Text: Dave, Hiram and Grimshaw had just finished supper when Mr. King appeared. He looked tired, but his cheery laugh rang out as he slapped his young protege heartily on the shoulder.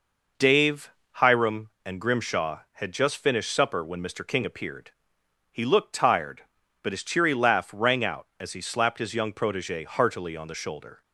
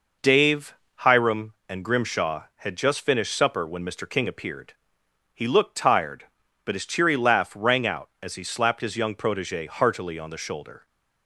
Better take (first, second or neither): neither